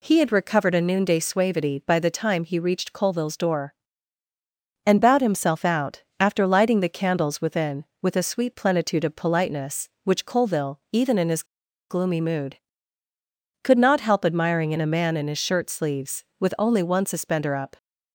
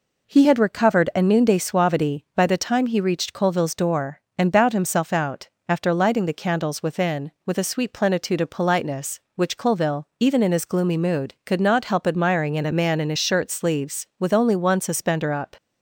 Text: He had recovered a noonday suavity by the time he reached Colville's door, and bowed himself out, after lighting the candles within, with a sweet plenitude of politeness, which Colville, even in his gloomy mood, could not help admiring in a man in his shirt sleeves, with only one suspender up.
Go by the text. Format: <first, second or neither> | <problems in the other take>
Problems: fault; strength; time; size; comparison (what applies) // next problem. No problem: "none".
second | pauses between "his" and "gloomy"; at 11.4 s; 0.45 s long